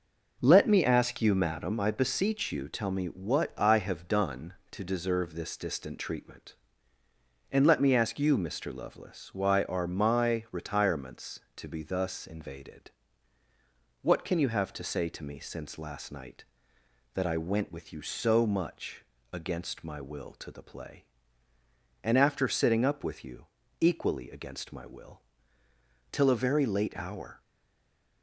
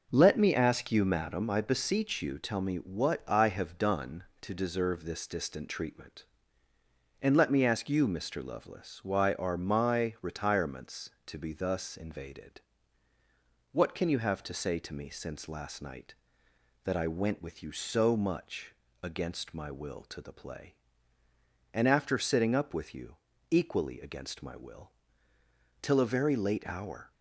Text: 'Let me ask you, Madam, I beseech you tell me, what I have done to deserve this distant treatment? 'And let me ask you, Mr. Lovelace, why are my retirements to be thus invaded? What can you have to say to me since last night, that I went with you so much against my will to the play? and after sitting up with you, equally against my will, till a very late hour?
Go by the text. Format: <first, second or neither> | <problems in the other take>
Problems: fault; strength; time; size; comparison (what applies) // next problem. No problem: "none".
second | pauses between "much" and "against"; slight; at 19.0 s; 0.30 s long; slight in the second // stays silent after the last word; slight; from 27.4 s on; 0.8 s long